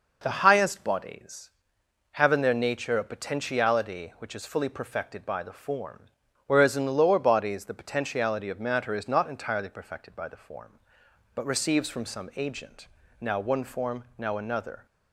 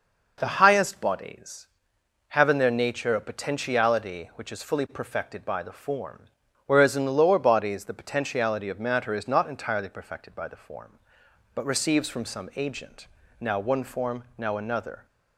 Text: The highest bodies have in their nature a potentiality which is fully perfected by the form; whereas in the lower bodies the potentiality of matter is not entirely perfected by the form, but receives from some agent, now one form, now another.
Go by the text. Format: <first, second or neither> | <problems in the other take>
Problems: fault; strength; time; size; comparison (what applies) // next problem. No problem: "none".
neither | none